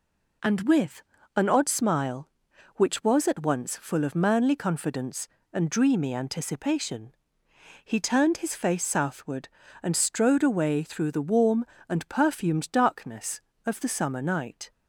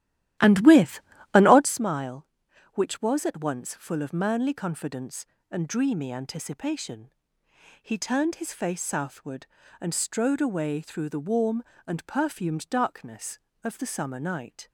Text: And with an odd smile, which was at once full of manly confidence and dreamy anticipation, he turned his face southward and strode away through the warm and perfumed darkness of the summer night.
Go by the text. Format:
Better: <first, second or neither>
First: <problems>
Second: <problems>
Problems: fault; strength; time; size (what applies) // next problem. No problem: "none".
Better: first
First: pauses between "with" and "an"; slight; at 1.0 s; 0.32 s long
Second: starts louder than the rest; strong; until 1.7 s; 13.5 dB // pauses between "with" and "an"; slight; at 1.0 s; 0.32 s long